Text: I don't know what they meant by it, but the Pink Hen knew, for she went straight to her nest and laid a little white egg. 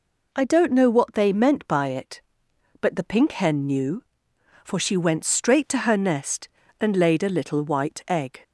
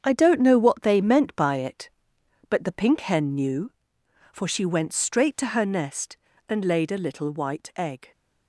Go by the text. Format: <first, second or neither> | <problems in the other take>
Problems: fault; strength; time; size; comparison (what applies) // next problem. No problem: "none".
first | gets quieter; strong; throughout; 8 dB